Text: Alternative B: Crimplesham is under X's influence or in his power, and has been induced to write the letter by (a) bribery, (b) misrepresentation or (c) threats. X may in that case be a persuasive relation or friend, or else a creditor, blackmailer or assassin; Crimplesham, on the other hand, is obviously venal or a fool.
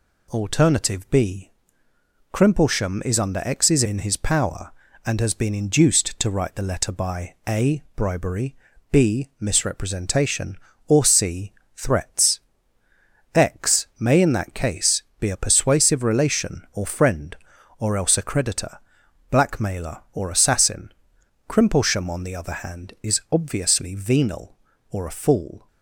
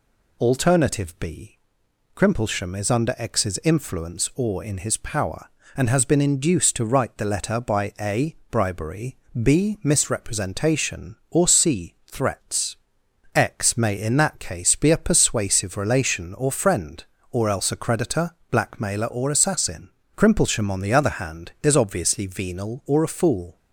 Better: second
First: skips "influence or"; at 3.8 s // pauses between "case" and "be"; slight; at 15.0 s; 0.16 s long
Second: none

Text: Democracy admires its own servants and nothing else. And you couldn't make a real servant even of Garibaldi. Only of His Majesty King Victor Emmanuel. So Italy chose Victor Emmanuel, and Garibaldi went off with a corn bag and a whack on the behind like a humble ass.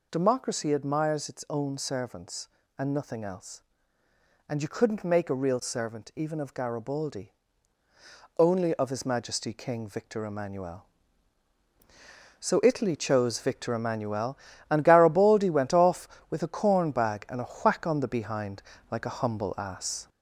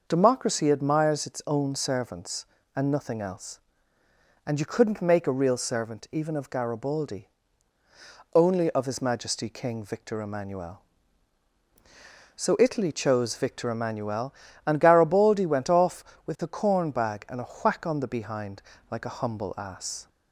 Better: second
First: gets louder; throughout; 3.5 dB // pauses between "behind" and "like"; slight; at 18.6 s; 0.28 s long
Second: pauses between "behind" and "like"; slight; at 18.6 s; 0.28 s long

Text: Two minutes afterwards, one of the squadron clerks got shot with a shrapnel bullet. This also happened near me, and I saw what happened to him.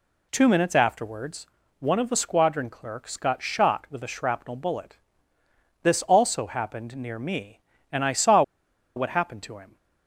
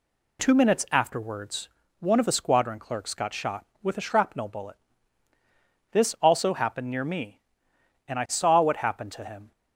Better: second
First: pauses between "saw" and "what"; noticeable; at 8.4 s; 0.53 s long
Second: none

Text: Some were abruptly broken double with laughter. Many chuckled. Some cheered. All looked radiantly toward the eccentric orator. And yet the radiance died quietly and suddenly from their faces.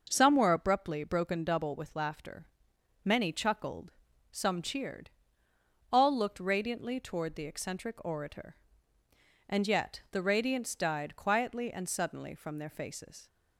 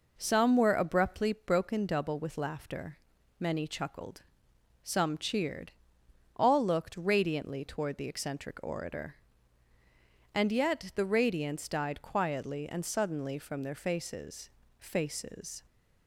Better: first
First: none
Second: says "faces" twice; at 14.7 s

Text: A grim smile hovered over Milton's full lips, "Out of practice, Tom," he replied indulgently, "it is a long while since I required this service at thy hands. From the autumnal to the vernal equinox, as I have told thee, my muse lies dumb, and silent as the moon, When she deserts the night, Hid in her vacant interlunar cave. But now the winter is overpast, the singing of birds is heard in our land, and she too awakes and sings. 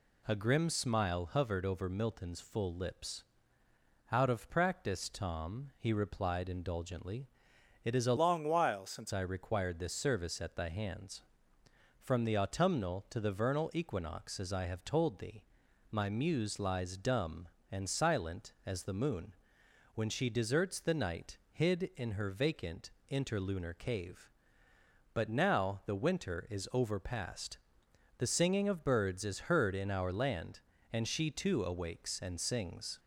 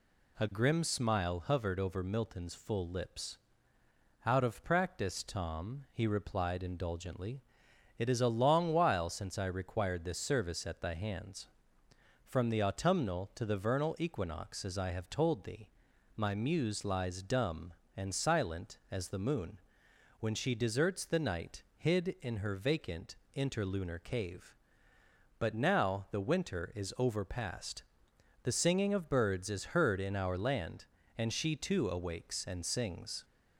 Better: second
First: changes voice from "long" to "since"; from 8.1 to 9.1 s; 1.0 s long // pauses between "vacant" and "interlunar"; slight; at 22.8 s; 0.22 s long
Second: pauses between "vacant" and "interlunar"; slight; at 23.1 s; 0.22 s long

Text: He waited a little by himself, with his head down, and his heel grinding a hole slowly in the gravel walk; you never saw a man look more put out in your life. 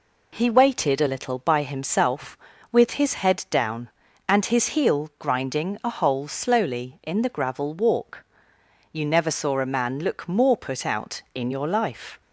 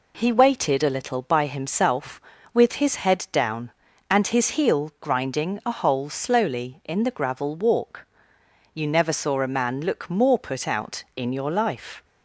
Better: neither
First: none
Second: none

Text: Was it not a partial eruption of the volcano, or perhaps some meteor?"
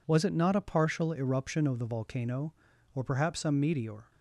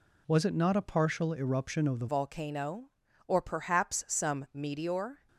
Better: first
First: none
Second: changes voice at "volcano"; from 2.0 s on; 3.2 s long

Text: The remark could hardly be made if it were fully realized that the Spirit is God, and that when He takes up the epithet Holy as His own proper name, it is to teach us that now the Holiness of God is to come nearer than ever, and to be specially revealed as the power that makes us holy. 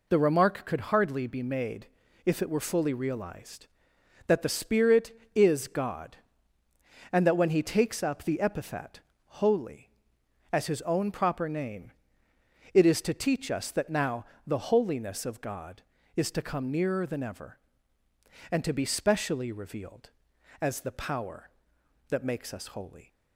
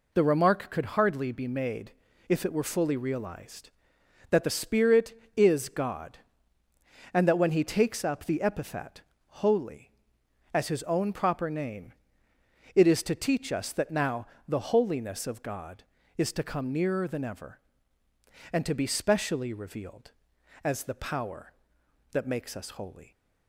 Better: neither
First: pauses between "made" and "if"; at 1.8 s; 0.38 s long // pauses between "epithet" and "Holy"; at 8.9 s; 0.40 s long // pauses between "now" and "the"; slight; at 14.2 s; 0.22 s long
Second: pauses between "made" and "if"; at 1.9 s; 0.36 s long // pauses between "epithet" and "Holy"; at 9.0 s; 0.40 s long // pauses between "now" and "the"; slight; at 14.2 s; 0.22 s long

